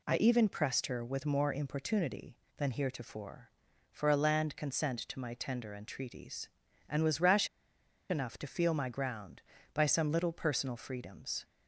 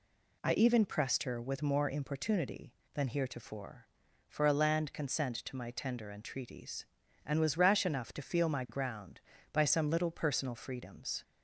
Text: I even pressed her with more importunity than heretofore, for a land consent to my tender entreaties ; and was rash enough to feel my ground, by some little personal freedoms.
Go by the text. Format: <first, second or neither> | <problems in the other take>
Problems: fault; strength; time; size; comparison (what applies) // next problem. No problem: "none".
second | pauses between "rash" and "enough"; noticeable; at 7.4 s; 0.62 s long